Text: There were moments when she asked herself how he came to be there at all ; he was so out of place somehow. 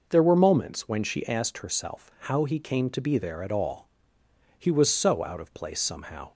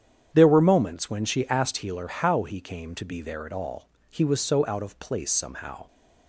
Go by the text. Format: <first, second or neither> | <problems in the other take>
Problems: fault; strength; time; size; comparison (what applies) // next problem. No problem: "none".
first | starts louder than the rest; strong; until 1.3 s; 9 dB // says "healer" for "herself"; at 1.7 s